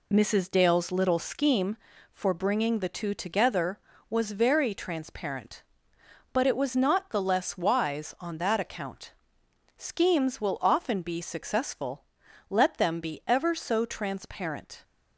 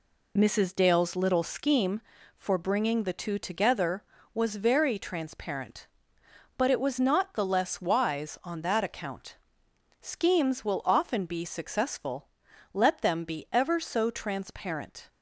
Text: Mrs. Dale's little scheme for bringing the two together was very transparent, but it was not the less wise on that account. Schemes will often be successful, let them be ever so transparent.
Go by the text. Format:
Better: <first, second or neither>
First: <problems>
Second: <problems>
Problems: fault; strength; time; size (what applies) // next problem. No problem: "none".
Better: neither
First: none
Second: none